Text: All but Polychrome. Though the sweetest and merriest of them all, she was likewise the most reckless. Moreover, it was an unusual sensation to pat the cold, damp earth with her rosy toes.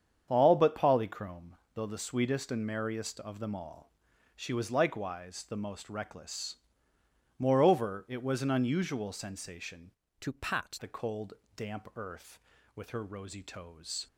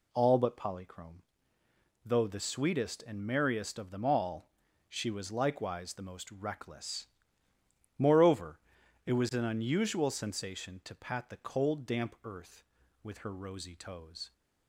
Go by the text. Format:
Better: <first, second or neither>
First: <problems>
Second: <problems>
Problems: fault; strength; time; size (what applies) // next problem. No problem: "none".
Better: second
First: starts louder than the rest; strong; until 1.2 s; 8 dB // changes voice from "to" to "pat"; from 10.2 to 10.7 s; 0.5 s long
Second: none